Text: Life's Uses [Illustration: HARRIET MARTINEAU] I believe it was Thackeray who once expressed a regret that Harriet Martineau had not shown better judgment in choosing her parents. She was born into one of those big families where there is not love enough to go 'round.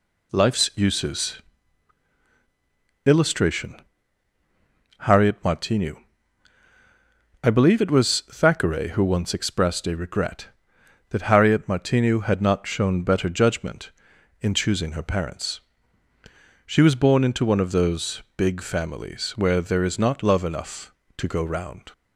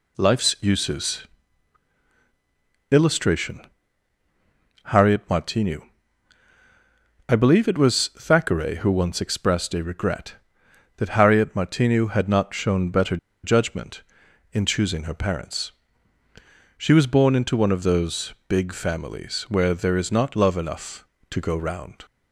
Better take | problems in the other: first | pauses between "Uses" and "Illustration"; strong; at 1.2 s; 1.6 s long; strong in the first // pauses between "MARTINEAU" and "I"; strong; at 5.8 s; 1.4 s long; strong in the first // pauses between "better" and "judgment"; slight; at 13.1 s; 0.26 s long

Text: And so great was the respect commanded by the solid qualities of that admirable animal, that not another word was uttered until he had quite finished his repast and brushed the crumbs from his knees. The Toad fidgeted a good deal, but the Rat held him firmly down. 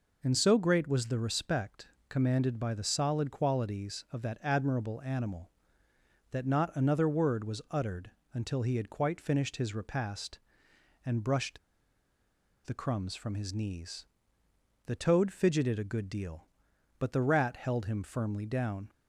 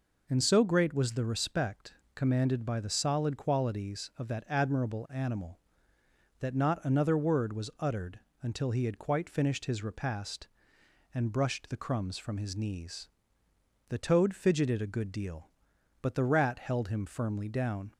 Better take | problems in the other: second | pauses between "respect" and "commanded"; slight; at 1.8 s; 0.22 s long; slight in the second // pauses between "uttered" and "until"; slight; at 8.1 s; 0.22 s long; slight in the second // pauses between "brushed" and "the"; at 11.5 s; 1.0 s long

